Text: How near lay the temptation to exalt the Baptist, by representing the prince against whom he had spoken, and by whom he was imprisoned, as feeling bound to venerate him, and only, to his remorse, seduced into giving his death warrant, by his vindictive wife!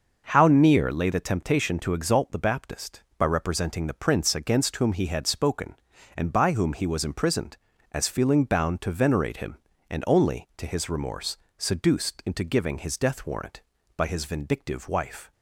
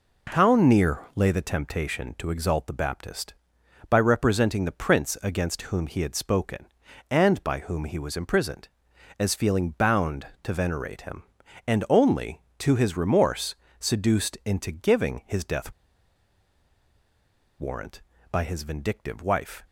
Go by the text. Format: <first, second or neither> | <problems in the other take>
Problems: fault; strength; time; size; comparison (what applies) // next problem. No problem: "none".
first | pauses between "near" and "lay"; slight; at 0.9 s; 0.16 s long // pauses between "death" and "warrant"; strong; at 15.7 s; 1.8 s long